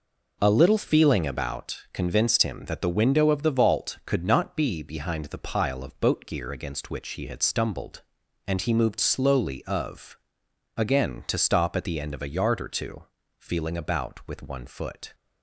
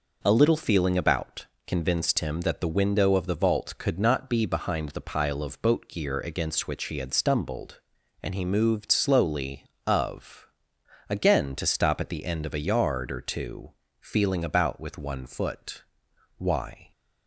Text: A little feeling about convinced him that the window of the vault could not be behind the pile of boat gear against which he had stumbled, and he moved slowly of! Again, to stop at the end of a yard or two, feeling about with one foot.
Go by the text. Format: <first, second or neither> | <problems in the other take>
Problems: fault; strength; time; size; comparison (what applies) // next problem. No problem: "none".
first | pauses between "about" and "convinced"; slight; at 1.4 s; 0.18 s long // goes on to say "Why"; from 16.3 s on; 0.54 s long